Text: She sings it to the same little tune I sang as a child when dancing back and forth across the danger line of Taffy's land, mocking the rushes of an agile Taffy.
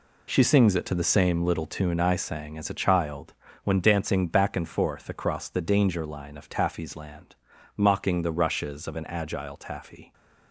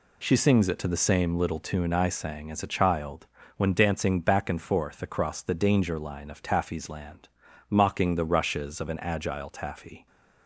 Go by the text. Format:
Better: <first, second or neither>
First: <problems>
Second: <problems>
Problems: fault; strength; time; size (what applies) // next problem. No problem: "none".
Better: second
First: gets quieter; strong; throughout; 9.5 dB // pauses between "child" and "when"; slight; at 3.3 s; 0.30 s long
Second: pauses between "child" and "when"; slight; at 3.2 s; 0.30 s long